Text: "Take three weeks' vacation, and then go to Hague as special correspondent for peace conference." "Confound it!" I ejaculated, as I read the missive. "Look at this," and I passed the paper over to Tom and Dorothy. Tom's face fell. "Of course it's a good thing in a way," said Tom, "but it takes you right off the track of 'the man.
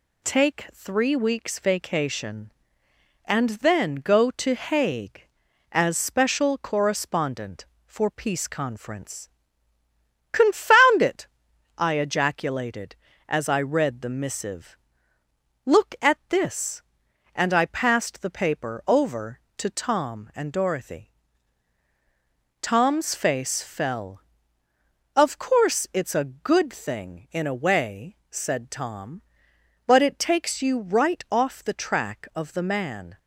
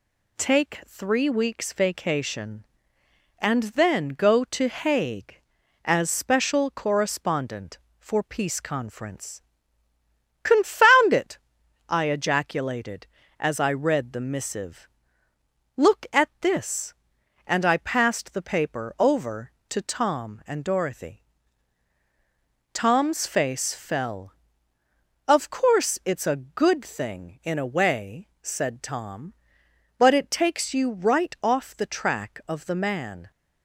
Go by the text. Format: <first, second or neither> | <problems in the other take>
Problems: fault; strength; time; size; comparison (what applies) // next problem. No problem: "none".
neither | none